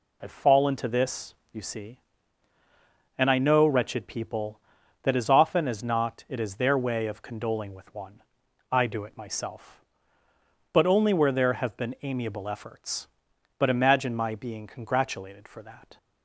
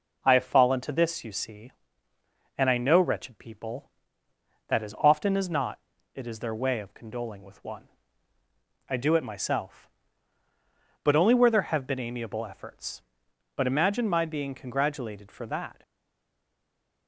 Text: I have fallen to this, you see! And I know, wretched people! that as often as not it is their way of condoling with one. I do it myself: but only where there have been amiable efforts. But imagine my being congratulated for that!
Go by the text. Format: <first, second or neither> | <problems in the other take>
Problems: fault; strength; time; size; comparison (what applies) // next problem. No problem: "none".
first | pauses between "not" and "it"; slight; at 5.8 s; 0.34 s long // stays silent after the last word; noticeable; from 15.8 s on; 1.2 s long